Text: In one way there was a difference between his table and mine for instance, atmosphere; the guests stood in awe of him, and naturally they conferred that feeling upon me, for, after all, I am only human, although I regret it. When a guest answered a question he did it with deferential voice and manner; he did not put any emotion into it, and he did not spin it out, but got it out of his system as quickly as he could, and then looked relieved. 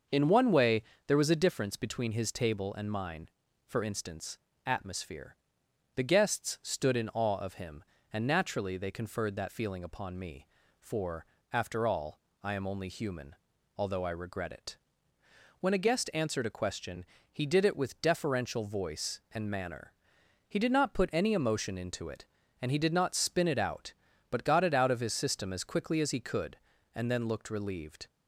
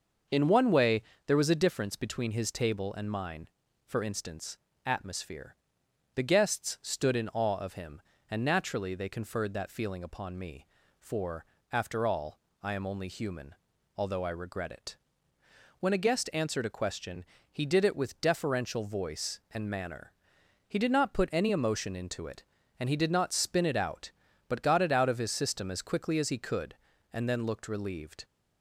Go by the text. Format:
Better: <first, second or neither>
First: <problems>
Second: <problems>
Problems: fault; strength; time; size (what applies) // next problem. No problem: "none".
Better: neither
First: starts louder than the rest; until 1.3 s; 6 dB // pauses between "way" and "there"; slight; at 0.8 s; 0.24 s long // pauses between "question" and "he"; slight; at 17.0 s; 0.28 s long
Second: starts louder than the rest; until 1.5 s; 6 dB // pauses between "way" and "there"; slight; at 1.0 s; 0.24 s long // pauses between "question" and "he"; slight; at 17.2 s; 0.28 s long